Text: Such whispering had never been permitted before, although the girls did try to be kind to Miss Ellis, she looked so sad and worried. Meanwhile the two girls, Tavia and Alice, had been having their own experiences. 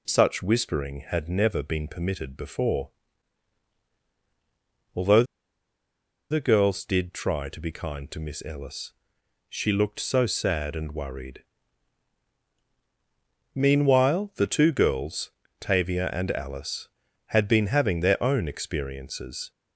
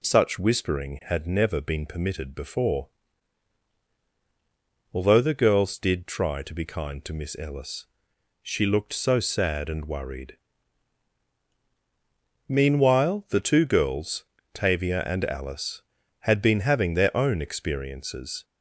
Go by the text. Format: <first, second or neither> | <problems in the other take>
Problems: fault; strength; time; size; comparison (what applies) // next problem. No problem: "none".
second | pauses between "although" and "the"; at 5.2 s; 1.0 s long